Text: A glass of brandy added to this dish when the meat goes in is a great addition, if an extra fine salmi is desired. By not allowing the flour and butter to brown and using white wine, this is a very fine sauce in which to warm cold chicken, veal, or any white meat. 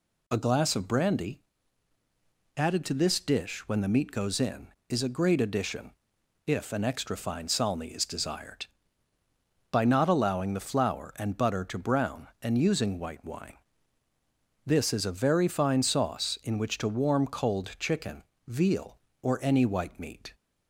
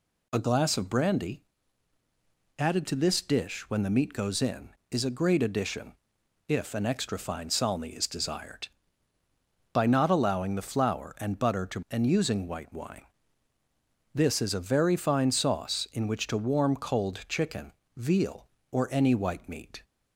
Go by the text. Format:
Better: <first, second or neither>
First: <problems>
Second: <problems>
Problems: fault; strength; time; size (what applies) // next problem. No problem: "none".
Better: first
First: pauses between "brandy" and "added"; at 1.3 s; 1.1 s long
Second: pauses between "brandy" and "added"; at 1.4 s; 1.1 s long // skips "brown"; at 11.8 s